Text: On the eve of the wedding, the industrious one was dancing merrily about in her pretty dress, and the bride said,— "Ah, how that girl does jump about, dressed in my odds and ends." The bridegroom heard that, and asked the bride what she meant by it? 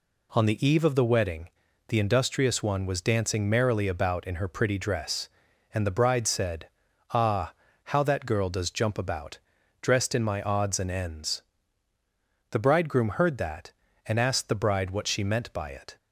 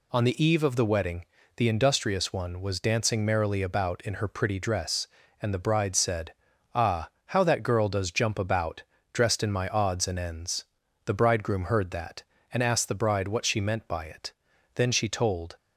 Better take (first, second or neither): first